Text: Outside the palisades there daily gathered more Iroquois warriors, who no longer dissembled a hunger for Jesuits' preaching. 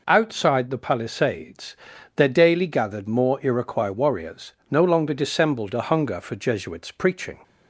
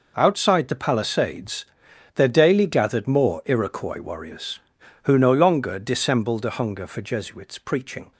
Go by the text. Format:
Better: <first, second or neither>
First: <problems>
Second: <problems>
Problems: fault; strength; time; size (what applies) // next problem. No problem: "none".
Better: second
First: pauses between "palisades" and "there"; at 1.7 s; 0.38 s long // skips "who"; at 4.6 s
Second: pauses between "palisades" and "there"; noticeable; at 1.6 s; 0.48 s long